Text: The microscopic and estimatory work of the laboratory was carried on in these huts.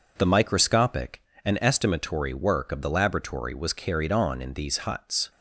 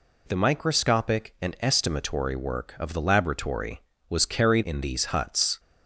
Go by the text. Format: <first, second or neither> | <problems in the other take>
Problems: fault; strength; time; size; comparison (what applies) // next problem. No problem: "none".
first | skips "on"; at 4.6 s